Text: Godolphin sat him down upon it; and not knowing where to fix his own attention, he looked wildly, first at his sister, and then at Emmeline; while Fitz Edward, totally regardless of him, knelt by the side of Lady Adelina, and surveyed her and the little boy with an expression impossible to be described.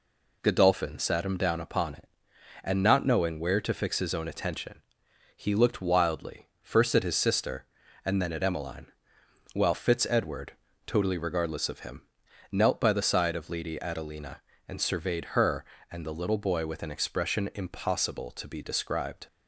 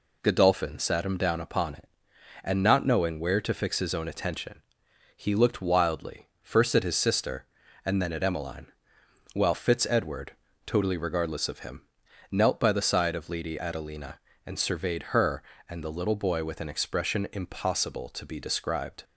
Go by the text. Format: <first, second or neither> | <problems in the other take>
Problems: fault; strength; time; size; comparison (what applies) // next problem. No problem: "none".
neither | none